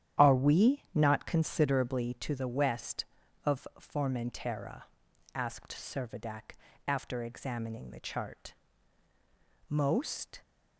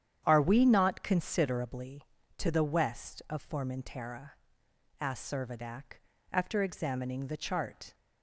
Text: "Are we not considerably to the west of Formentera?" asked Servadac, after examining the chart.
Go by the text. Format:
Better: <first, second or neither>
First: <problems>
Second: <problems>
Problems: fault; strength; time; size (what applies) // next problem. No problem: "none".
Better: second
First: starts louder than the rest; strong; until 1.2 s; 10.5 dB // goes on to say "Most"; noticeable; from 9.6 s on; 0.72 s long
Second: starts louder than the rest; strong; until 1.2 s; 9.5 dB